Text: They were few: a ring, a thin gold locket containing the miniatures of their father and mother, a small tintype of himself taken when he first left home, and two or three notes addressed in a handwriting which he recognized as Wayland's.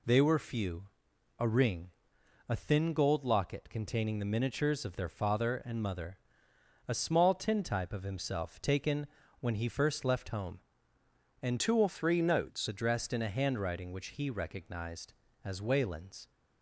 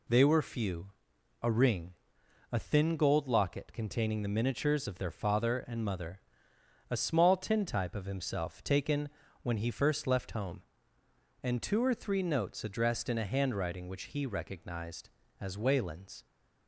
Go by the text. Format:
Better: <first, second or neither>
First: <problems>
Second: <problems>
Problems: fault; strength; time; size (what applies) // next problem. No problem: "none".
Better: second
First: pauses between "taken" and "when"; slight; at 9.0 s; 0.34 s long // changes voice from "two" to "notes"; from 11.5 to 12.6 s; 1.1 s long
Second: pauses between "taken" and "when"; slight; at 9.0 s; 0.34 s long